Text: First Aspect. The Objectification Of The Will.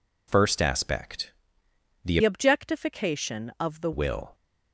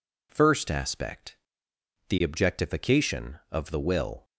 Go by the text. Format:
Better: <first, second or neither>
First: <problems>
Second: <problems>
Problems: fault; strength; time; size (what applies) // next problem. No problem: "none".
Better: second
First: changes voice from "Objectification" to "The"; from 2.2 to 3.9 s; 1.7 s long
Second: none